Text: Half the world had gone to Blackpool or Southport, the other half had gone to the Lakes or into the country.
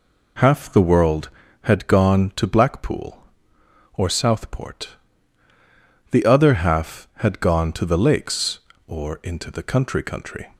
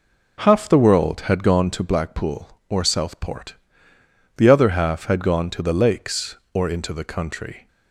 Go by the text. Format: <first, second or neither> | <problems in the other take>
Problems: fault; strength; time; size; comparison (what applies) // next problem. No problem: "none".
second | says "country" twice; at 10.0 s